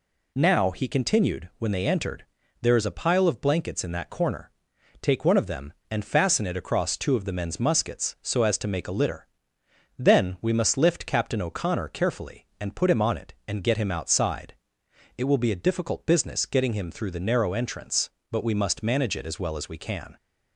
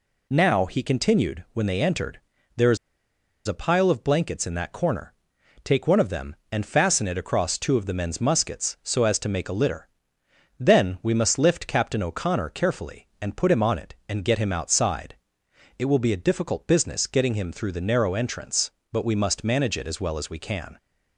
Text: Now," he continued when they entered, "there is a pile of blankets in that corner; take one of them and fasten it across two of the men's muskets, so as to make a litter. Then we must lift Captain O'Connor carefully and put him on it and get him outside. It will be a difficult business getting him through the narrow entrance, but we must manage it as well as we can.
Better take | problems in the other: first | pauses between "is" and "a"; noticeable; at 2.7 s; 0.69 s long

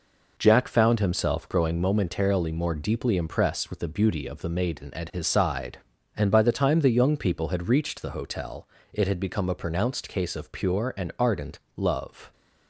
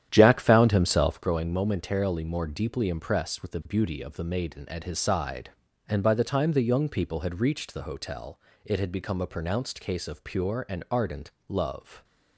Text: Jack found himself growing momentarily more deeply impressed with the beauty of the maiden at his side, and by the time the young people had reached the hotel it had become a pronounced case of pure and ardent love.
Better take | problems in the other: first | starts louder than the rest; strong; until 1.3 s; 10 dB // pauses between "hotel" and "it"; slight; at 8.3 s; 0.28 s long; slight in the first // pauses between "ardent" and "love"; slight; at 11.3 s; 0.16 s long; slight in the first

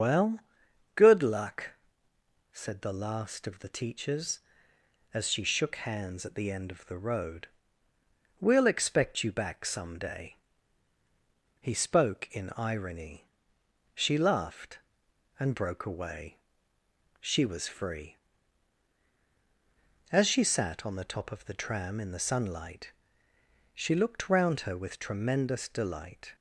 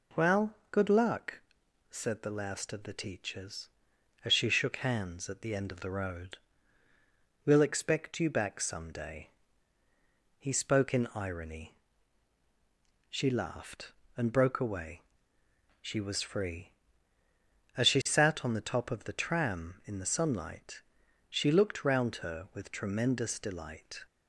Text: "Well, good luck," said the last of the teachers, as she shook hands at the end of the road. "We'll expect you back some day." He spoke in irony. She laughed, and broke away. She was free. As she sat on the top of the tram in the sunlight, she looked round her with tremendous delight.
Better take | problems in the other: second | loses the start of "Well"; at 0.0 s; 105 ms // starts louder than the rest; until 1.5 s; 6.5 dB

